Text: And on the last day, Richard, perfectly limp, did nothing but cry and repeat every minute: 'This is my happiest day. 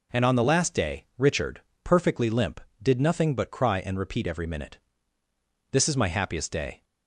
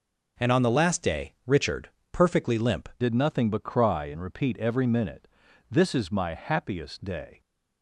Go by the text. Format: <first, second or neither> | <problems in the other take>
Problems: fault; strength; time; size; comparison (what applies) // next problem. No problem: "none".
first | changes voice at "did"; from 3.0 s on; 4.4 s long